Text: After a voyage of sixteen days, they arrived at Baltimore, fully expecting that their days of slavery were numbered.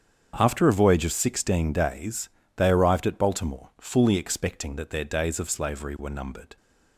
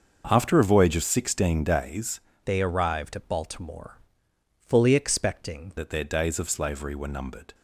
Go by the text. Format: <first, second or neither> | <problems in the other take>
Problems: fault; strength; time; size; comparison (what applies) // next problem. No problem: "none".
first | starts louder than the rest; until 1.2 s; 6 dB; strong in the first // changes voice from "they" to "expecting"; from 2.4 to 5.7 s; 3.3 s long